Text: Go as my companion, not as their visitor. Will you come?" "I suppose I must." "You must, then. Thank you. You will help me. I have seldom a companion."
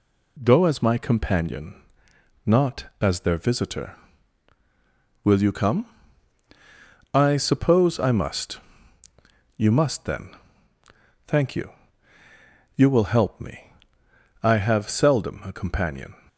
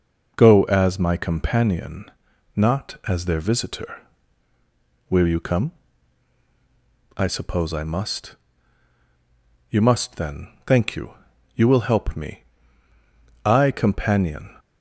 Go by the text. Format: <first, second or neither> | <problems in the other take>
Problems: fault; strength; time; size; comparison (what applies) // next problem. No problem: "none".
first | skips "have seldom a"; at 13.7 s